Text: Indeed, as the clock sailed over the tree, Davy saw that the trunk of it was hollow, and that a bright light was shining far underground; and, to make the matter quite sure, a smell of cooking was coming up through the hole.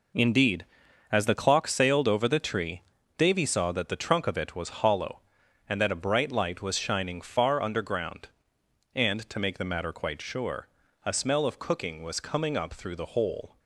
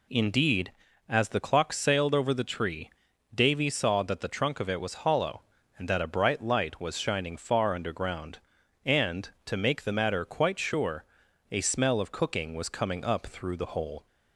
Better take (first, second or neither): neither